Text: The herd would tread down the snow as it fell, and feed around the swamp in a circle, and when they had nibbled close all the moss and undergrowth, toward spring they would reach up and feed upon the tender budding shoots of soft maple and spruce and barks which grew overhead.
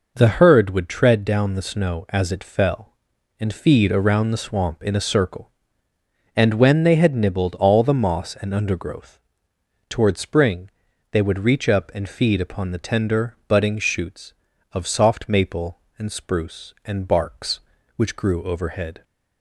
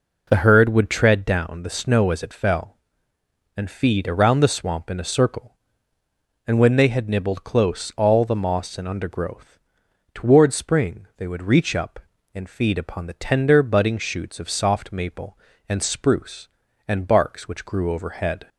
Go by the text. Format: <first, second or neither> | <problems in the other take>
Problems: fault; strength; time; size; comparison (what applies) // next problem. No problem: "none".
second | skips "close"; at 7.5 s // pauses between "spring" and "they"; at 10.6 s; 0.42 s long